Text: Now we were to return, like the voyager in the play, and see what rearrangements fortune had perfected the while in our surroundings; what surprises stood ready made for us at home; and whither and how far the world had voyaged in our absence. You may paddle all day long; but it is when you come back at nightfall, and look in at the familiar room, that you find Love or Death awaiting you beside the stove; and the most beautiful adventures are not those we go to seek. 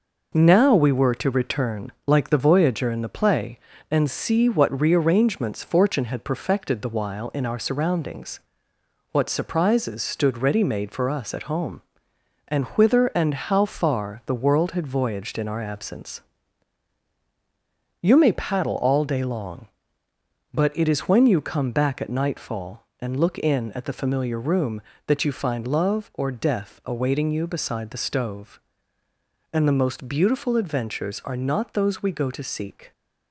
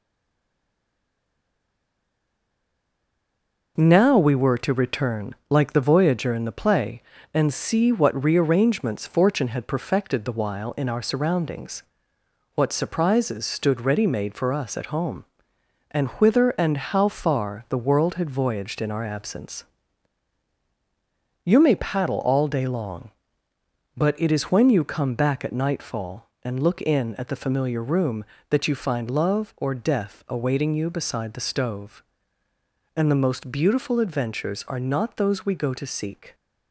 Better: first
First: none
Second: stays silent before the first word; strong; until 3.7 s; 3.7 s long

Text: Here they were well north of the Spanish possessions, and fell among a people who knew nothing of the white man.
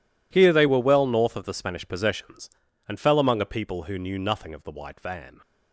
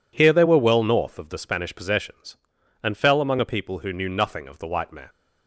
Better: second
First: says "van" for "man"; at 4.9 s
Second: none

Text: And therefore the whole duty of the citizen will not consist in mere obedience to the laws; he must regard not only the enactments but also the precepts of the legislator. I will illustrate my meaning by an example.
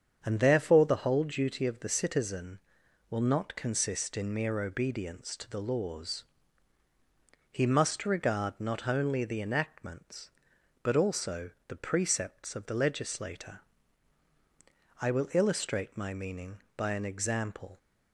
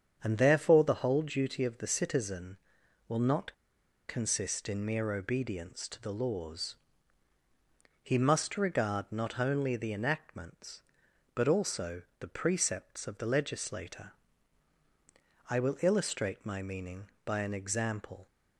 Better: first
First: starts louder than the rest; strong; until 1.2 s; 7.5 dB // pauses between "also" and "the"; slight; at 11.5 s; 0.16 s long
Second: starts louder than the rest; strong; until 1.2 s; 7.5 dB // pauses between "not" and "consist"; noticeable; at 3.5 s; 0.55 s long // pauses between "also" and "the"; slight; at 12.0 s; 0.16 s long

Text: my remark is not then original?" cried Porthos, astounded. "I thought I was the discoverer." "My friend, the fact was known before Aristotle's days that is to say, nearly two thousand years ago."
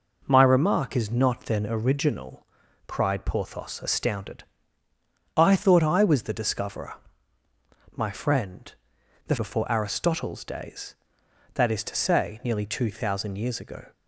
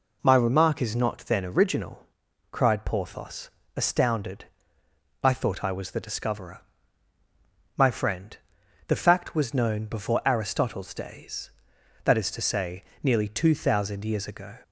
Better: second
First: skips "fact was known"; at 9.3 s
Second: none

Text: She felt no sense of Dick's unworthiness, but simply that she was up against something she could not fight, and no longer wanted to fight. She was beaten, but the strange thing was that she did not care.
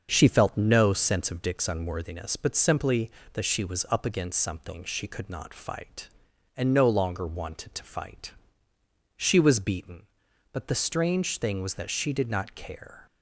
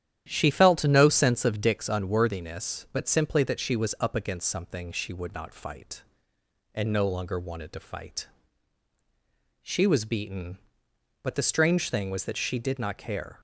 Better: first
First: starts louder than the rest; until 1.1 s; 6.5 dB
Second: starts louder than the rest; strong; until 1.2 s; 10.5 dB // says "would" for "could"; at 5.1 s

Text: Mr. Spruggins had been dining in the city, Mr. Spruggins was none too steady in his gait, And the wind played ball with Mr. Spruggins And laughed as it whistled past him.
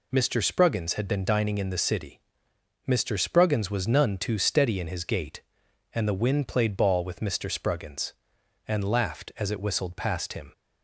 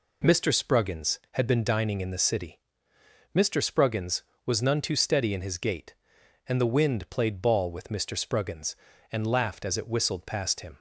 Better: neither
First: none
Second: none

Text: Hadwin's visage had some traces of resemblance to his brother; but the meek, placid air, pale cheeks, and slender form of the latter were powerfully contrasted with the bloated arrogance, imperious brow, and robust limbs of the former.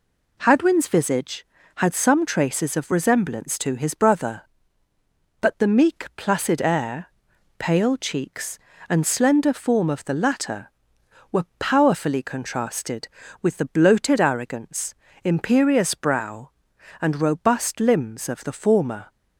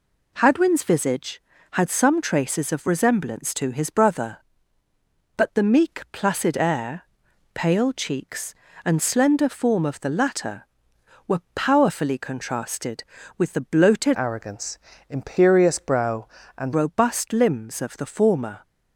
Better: first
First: none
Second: changes voice from "arrogance" to "and"; from 14.1 to 16.7 s; 2.6 s long

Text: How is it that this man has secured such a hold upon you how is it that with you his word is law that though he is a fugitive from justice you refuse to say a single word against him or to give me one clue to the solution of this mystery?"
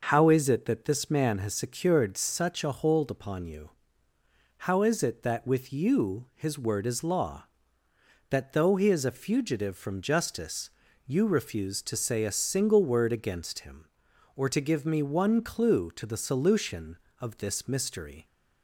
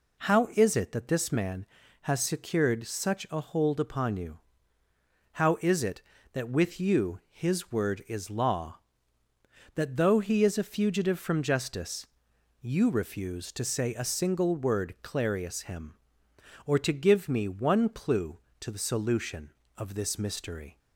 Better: first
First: pauses between "you" and "how"; noticeable; at 3.6 s; 0.98 s long // pauses between "justice" and "you"; at 10.6 s; 0.38 s long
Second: pauses between "you" and "how"; noticeable; at 4.3 s; 0.94 s long // pauses between "justice" and "you"; noticeable; at 12.0 s; 0.54 s long // says "clarius" for "against"; at 15.0 s

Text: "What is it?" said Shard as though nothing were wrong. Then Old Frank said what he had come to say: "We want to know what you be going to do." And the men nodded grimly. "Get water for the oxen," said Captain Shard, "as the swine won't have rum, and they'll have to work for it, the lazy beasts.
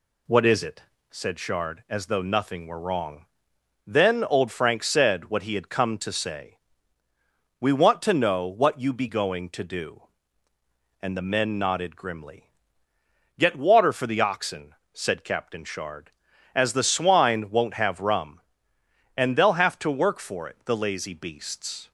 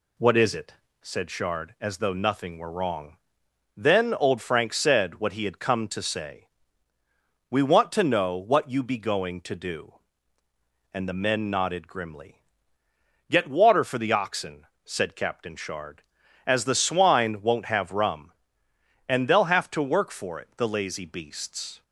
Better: neither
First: none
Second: none

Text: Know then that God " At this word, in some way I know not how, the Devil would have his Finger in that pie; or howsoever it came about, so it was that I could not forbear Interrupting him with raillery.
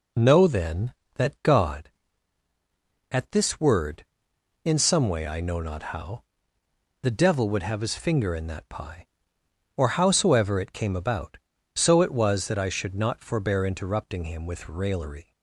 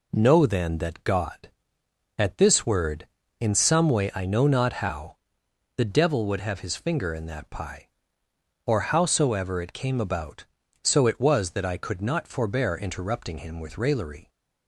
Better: second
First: says "should" for "could"; at 12.6 s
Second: none

